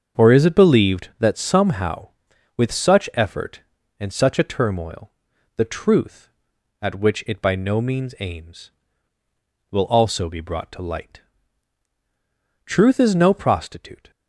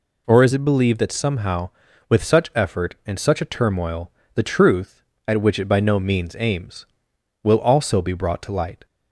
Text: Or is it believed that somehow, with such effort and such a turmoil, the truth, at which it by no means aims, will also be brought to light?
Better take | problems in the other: second | starts louder than the rest; until 1.2 s; 6.5 dB // goes on to say "Truth is no prostitute"; from 12.6 s on; 1.4 s long

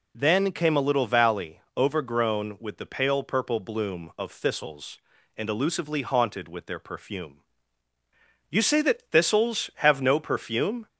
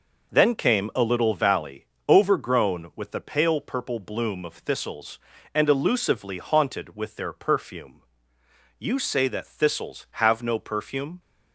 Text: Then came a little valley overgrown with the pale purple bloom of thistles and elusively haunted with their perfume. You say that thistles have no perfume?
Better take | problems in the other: neither | pauses between "valley" and "overgrown"; slight; the same in both

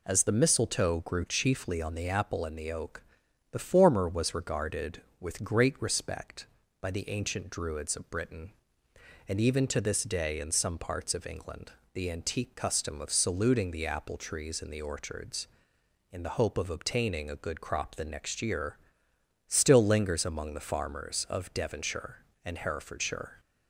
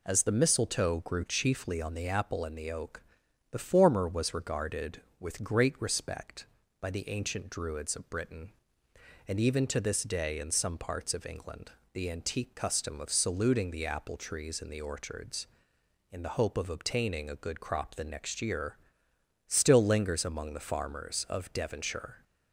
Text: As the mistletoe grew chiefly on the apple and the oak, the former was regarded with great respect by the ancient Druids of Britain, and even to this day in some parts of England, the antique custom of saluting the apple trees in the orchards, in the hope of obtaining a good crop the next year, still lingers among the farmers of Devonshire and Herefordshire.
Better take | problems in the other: first | stops before "and Herefordshire"; at 22.2 s

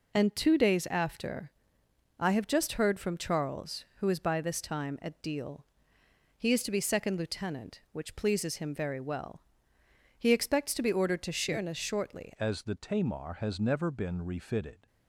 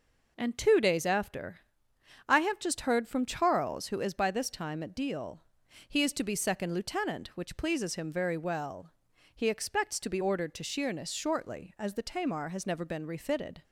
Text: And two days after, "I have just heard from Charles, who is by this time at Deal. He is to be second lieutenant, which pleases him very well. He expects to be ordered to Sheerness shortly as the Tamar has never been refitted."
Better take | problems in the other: second | changes voice at "as"; from 12.3 s on; 2.5 s long

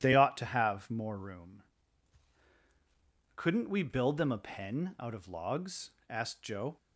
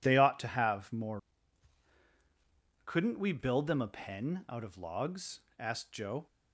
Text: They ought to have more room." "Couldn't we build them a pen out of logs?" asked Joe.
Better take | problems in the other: first | skips "room"; at 2.0 s

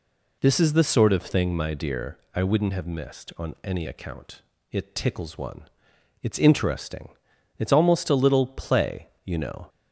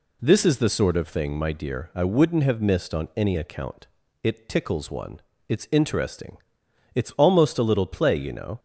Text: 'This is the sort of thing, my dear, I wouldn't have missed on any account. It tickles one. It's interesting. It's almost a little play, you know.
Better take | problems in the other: neither | none

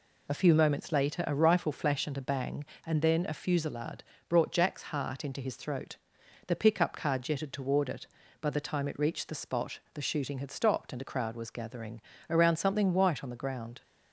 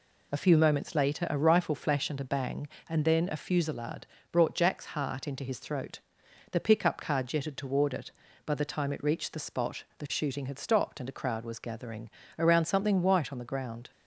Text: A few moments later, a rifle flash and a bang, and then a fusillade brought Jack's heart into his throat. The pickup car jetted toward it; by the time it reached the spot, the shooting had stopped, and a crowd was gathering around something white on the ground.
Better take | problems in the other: neither | pauses between "fusillade" and "brought"; slight; the same in both // pauses between "gathering" and "around"; slight; the same in both

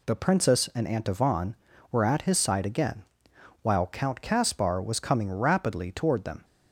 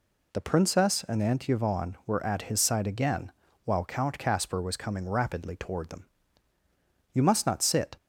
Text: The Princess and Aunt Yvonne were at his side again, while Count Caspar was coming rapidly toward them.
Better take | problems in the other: first | goes on to say "You must not sit"; noticeable; from 7.1 s on; 0.81 s long

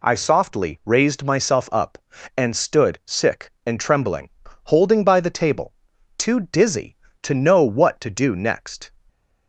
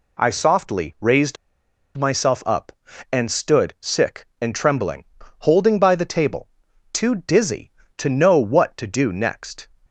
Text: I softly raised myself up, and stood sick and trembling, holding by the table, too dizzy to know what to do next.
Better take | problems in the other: first | pauses between "raised" and "myself"; noticeable; at 1.3 s; 0.60 s long

